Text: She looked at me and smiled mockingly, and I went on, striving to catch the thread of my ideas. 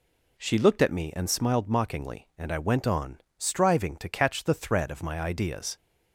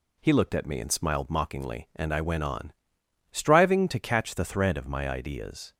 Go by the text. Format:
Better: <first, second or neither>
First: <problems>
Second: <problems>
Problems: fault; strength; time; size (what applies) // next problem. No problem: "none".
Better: first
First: none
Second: says "He" for "She"; at 0.1 s